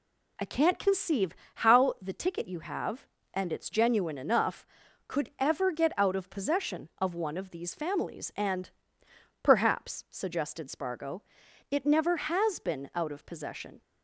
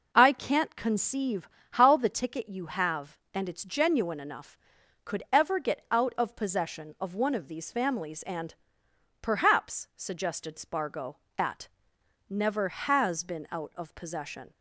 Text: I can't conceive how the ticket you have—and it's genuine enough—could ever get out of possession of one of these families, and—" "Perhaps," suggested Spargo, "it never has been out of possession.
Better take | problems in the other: first | pauses between "conceive" and "how"; slight; at 1.4 s; 0.24 s long; slight in the first // says "at" for "it"; at 11.3 s

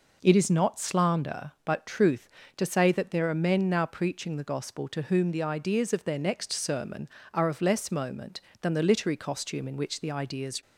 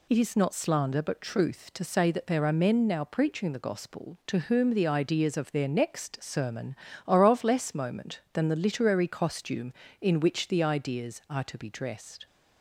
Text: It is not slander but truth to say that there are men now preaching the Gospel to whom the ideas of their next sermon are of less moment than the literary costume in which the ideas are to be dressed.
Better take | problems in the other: second | stops before "are to be dressed"; at 10.6 s

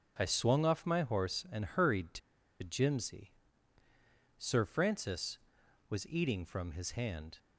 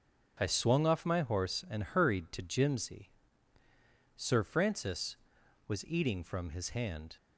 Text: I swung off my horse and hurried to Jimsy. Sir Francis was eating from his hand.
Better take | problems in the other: second | starts louder than the rest; until 1.1 s; 6 dB; also in the second // pauses between "to" and "Jimsy"; at 2.1 s; 0.43 s long

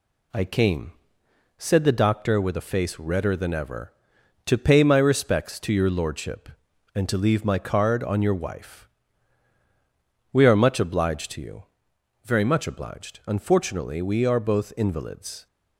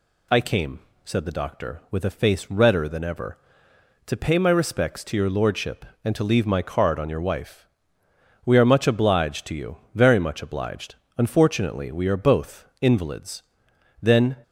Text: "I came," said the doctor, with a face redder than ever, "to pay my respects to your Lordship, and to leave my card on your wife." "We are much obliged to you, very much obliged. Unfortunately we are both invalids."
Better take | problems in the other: first | goes on to say "Then"; slight; from 14.0 s on; 0.34 s long

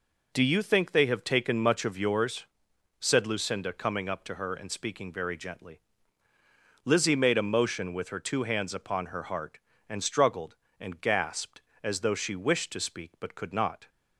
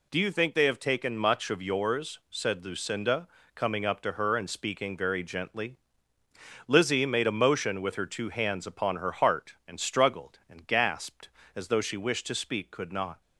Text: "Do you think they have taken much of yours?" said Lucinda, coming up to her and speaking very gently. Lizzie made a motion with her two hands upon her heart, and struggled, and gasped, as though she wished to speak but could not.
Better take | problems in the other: first | skips "but"; at 12.7 s

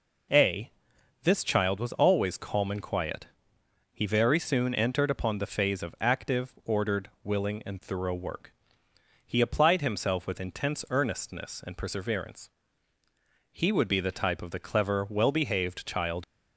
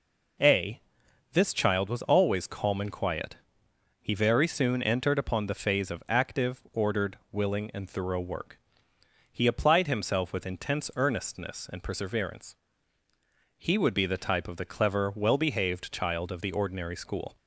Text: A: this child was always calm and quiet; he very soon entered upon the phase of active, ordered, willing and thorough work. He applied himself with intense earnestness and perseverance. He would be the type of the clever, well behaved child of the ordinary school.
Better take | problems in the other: second | stops before "of the ordinary school"; at 16.2 s

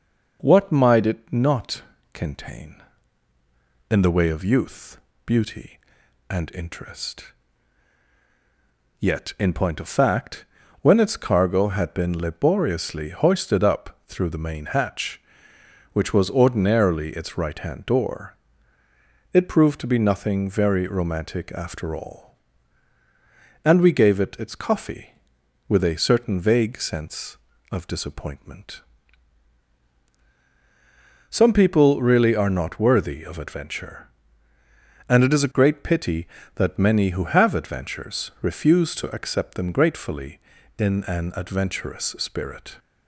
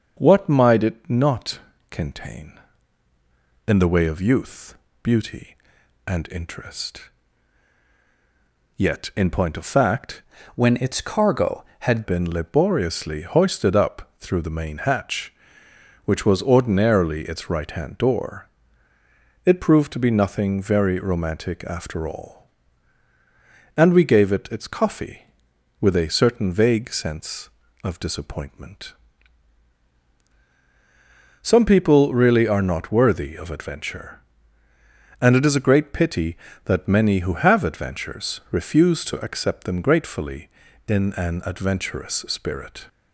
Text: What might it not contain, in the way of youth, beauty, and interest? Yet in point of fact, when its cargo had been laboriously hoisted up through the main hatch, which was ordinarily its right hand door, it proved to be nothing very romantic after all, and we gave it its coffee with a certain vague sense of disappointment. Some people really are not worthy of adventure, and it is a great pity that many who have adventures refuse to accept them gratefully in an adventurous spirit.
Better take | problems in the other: first | starts louder than the rest; until 1.1 s; 6 dB // pauses between "not" and "contain"; slight; at 1.5 s; 0.32 s long; slight in the first // changes voice from "when" to "had"; from 10.5 to 12.0 s; 1.5 s long

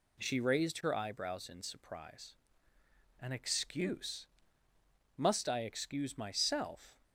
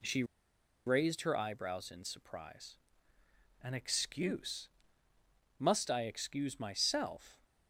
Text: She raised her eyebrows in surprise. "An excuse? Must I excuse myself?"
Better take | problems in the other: first | pauses between "She" and "raised"; noticeable; at 0.2 s; 0.62 s long

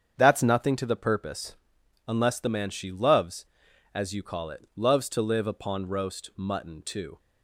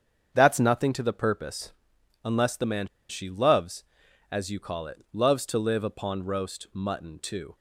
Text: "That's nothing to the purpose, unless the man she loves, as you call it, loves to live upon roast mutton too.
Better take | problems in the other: first | starts louder than the rest; strong; until 1.3 s; 7.5 dB; strong in the first // pauses between "man" and "she"; slight; at 2.8 s; 0.23 s long

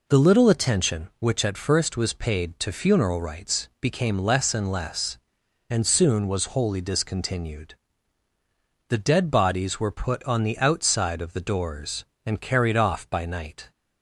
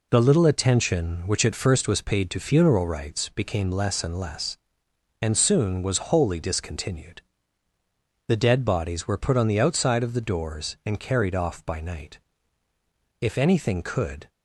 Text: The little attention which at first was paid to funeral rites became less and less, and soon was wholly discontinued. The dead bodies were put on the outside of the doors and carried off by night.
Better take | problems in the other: first | goes on to say "If anything could"; noticeable; from 13.2 s on; 1.0 s long

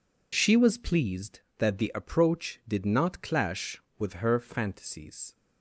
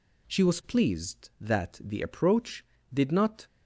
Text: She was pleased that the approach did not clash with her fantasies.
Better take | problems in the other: first | stops before "clash with her fantasies"; at 3.4 s

